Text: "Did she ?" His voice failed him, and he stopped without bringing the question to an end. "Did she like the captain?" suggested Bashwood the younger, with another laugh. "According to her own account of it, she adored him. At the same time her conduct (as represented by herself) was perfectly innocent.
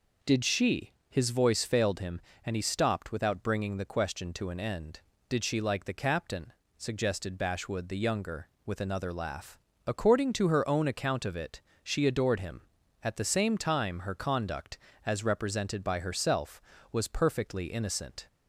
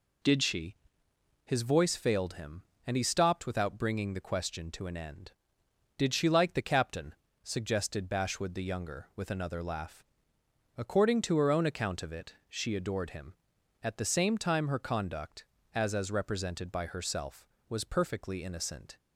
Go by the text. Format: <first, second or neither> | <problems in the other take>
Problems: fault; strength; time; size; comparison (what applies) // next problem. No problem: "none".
first | says "as" twice; at 15.9 s